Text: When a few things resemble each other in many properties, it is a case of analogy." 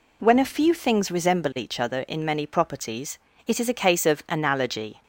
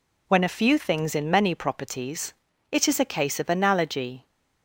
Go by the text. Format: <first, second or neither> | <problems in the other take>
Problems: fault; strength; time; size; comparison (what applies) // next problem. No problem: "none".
first | skips "resemble each other"; at 1.1 s